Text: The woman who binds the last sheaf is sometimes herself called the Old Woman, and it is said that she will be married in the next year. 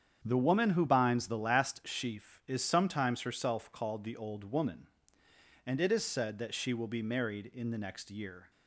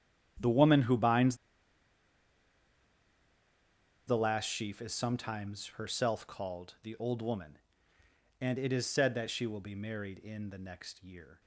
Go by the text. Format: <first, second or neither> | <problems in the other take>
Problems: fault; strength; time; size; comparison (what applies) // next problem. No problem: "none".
first | starts louder than the rest; strong; until 4.1 s; 10 dB; strong in the first // pauses between "binds" and "the"; strong; at 1.3 s; 2.7 s long